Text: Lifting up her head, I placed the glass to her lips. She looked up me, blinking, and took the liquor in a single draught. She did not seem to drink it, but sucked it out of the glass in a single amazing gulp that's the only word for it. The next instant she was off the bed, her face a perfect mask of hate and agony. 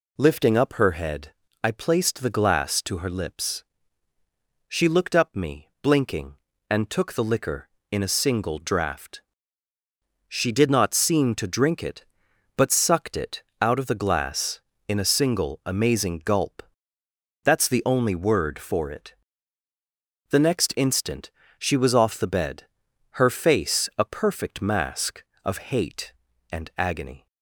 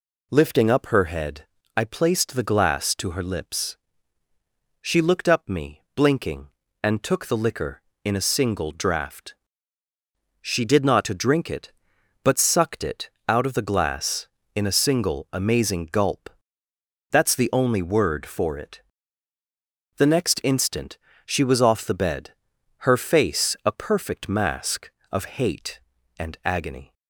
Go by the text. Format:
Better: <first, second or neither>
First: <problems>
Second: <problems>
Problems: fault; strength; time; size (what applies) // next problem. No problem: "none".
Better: first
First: pauses between "it" and "out"; slight; at 13.4 s; 0.20 s long // pauses between "gulp" and "that's"; noticeable; at 16.6 s; 0.82 s long // pauses between "instant" and "she"; slight; at 21.3 s; 0.26 s long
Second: skips "seem"; at 11.0 s // pauses between "it" and "out"; slight; at 13.0 s; 0.20 s long // pauses between "gulp" and "that's"; noticeable; at 16.2 s; 0.82 s long // pauses between "instant" and "she"; slight; at 20.9 s; 0.26 s long